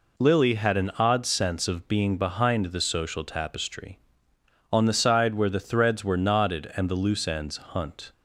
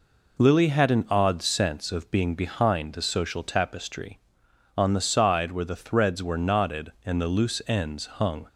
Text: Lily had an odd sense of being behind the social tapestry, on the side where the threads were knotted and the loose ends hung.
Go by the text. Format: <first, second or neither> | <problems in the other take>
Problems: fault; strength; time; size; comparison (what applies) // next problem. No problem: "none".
second | says "hunt" for "hung"; at 7.5 s